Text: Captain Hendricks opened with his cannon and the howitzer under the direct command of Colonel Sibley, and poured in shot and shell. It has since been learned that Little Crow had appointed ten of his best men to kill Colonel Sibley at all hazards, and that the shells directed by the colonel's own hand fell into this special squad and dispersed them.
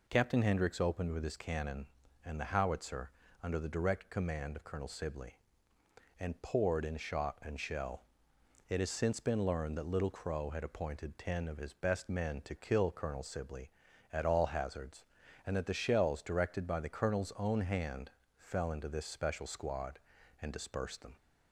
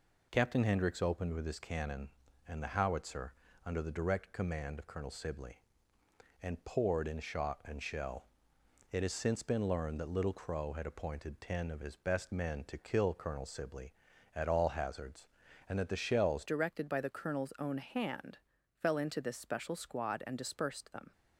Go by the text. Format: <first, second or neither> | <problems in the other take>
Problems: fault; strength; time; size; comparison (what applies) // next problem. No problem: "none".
first | pauses between "howitzer" and "under"; slight; at 3.3 s; 0.32 s long; slight in the first // changes voice at "directed"; from 16.4 s on; 4.7 s long // pauses between "hand" and "fell"; at 18.3 s; 0.40 s long; slight in the first